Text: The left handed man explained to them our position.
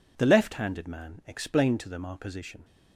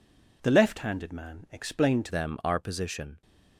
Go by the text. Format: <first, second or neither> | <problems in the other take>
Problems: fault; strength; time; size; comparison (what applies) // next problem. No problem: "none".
first | changes voice at "them"; from 2.0 s on; 1.2 s long